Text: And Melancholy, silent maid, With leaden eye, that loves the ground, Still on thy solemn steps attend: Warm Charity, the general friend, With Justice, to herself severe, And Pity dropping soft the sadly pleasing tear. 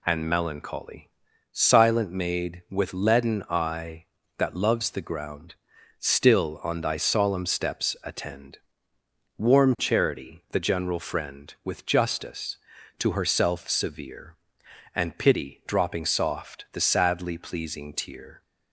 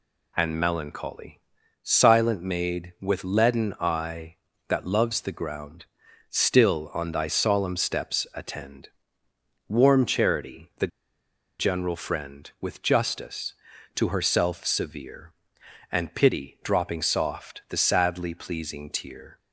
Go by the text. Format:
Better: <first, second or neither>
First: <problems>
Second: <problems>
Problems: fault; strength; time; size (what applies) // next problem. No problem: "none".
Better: first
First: none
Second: pauses between "the" and "general"; noticeable; at 10.8 s; 0.72 s long